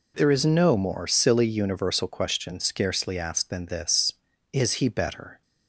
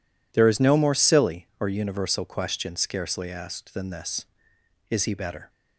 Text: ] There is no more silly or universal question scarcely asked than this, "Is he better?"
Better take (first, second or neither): second